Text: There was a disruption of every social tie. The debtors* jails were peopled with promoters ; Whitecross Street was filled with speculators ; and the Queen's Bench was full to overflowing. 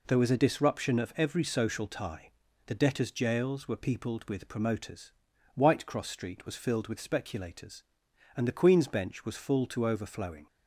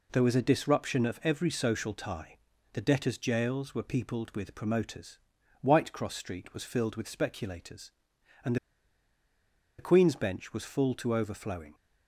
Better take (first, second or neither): first